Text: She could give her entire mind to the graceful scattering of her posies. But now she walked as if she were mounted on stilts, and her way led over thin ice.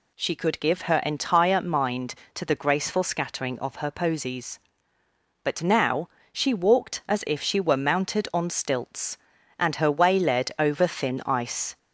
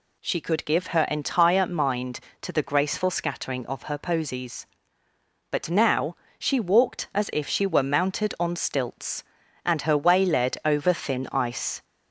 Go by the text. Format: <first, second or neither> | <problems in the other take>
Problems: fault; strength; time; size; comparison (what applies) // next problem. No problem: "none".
neither | pauses between "now" and "she"; slight; the same in both